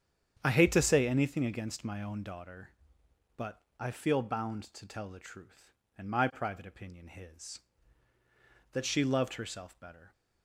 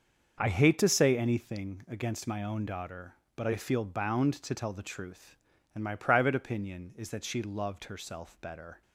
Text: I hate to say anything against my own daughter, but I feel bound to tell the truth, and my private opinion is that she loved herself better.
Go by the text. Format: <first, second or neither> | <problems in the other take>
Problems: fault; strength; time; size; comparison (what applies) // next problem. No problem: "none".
second | starts louder than the rest; strong; until 1.4 s; 8.5 dB; noticeable in the second // pauses between "but" and "I"; slight; at 3.5 s; 0.22 s long // says "his" for "is"; at 7.0 s